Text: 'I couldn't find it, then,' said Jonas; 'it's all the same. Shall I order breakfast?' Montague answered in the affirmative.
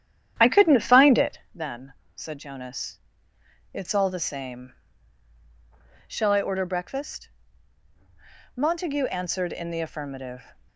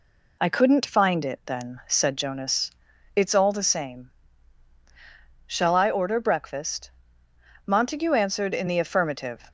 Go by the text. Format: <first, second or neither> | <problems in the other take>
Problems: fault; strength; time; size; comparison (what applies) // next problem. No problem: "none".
second | starts louder than the rest; strong; until 1.6 s; 10 dB